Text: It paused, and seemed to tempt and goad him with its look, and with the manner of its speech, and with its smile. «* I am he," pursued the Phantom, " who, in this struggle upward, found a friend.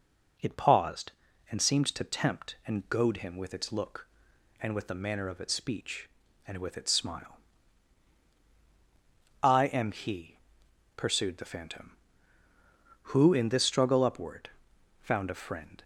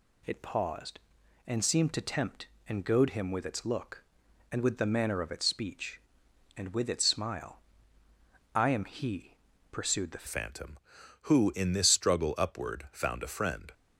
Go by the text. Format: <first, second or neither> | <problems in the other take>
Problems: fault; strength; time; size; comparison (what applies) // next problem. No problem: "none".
first | changes voice at "Phantom"; from 10.2 s on; 3.5 s long